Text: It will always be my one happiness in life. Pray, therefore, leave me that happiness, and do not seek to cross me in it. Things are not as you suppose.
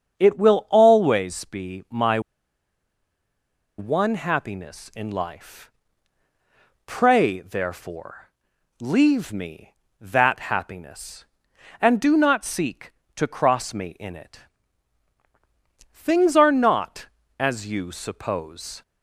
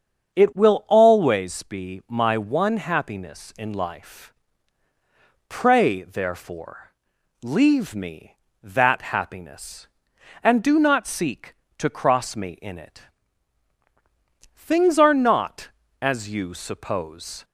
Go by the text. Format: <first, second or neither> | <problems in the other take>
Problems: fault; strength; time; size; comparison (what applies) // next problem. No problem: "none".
second | starts louder than the rest; until 1.2 s; 7 dB; also in the second // pauses between "my" and "one"; strong; at 2.1 s; 1.5 s long